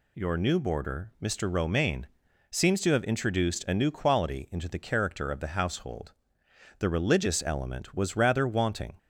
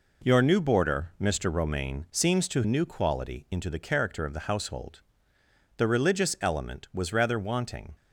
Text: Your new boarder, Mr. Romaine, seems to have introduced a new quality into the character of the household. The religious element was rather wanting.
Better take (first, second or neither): first